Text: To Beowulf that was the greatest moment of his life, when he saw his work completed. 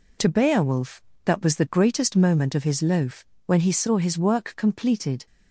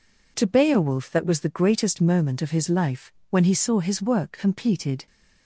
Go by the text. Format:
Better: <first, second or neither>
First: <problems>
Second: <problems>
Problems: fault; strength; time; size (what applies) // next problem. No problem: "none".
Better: second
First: says "loaf" for "life"; at 2.8 s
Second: none